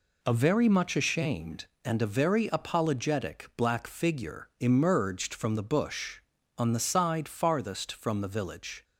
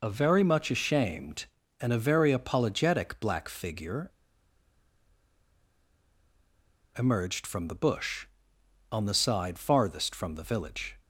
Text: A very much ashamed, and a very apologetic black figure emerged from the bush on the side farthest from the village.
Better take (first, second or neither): first